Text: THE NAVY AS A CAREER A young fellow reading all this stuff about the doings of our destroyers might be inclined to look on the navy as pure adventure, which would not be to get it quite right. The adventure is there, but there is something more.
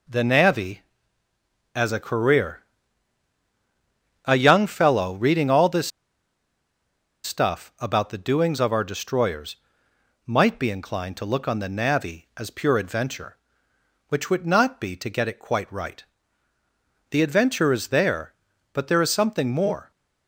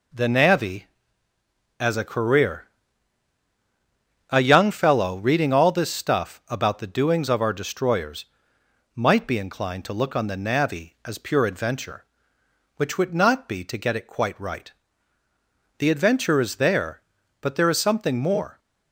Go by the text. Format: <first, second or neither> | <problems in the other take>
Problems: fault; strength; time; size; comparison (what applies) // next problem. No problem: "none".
second | pauses between "CAREER" and "A"; strong; at 2.6 s; 1.6 s long; strong in the second // pauses between "this" and "stuff"; strong; at 5.9 s; 1.3 s long // pauses between "destroyers" and "might"; noticeable; at 9.5 s; 0.70 s long; noticeable in the second